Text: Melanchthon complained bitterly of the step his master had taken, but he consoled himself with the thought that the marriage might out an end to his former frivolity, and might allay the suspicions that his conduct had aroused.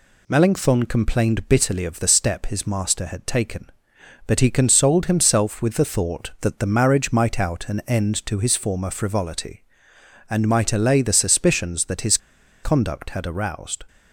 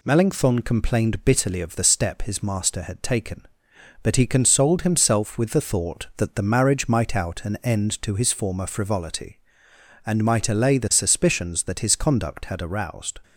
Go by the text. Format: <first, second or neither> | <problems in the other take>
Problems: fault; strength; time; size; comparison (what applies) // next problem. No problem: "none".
second | pauses between "his" and "conduct"; noticeable; at 12.1 s; 0.46 s long